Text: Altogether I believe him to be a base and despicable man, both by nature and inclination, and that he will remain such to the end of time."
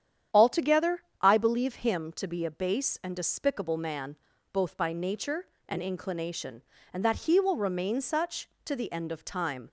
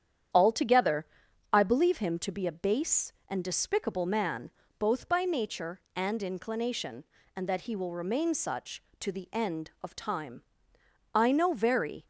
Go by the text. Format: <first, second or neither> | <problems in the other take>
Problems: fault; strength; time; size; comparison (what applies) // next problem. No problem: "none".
first | starts louder than the rest; strong; until 1.8 s; 9 dB; strong in the first // pauses between "Altogether" and "I"; noticeable; at 1.0 s; 0.46 s long; slight in the first // goes on to say "I know very"; noticeable; from 11.1 s on; 0.92 s long